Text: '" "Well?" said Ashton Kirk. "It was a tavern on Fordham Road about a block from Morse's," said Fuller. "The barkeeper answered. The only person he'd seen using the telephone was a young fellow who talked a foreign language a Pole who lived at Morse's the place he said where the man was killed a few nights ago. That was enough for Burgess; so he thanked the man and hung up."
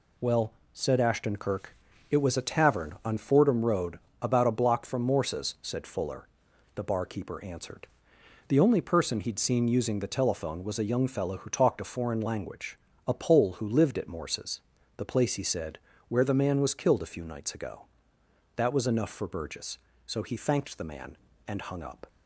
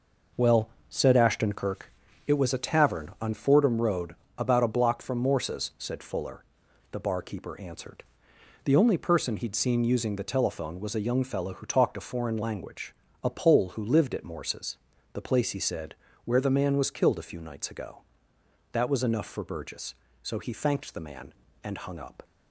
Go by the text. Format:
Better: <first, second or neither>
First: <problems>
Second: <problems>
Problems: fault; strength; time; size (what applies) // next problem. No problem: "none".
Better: first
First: pauses between "Road" and "about"; slight; at 3.9 s; 0.20 s long // pauses between "language" and "a"; slight; at 12.7 s; 0.28 s long // pauses between "Morse's" and "the"; slight; at 14.5 s; 0.36 s long // pauses between "said" and "where"; slight; at 15.7 s; 0.30 s long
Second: starts louder than the rest; noticeable; until 1.6 s; 5.5 dB // pauses between "Road" and "about"; slight; at 4.1 s; 0.20 s long // pauses between "language" and "a"; slight; at 12.9 s; 0.28 s long // pauses between "Morse's" and "the"; slight; at 14.7 s; 0.36 s long // pauses between "said" and "where"; slight; at 15.9 s; 0.30 s long